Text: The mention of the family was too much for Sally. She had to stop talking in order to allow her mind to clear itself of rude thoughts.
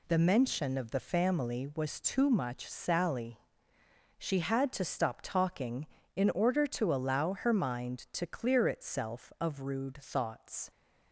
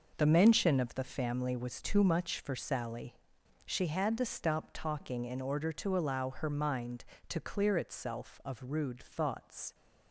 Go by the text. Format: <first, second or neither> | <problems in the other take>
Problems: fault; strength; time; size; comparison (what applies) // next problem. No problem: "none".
second | skips "for"; at 2.6 s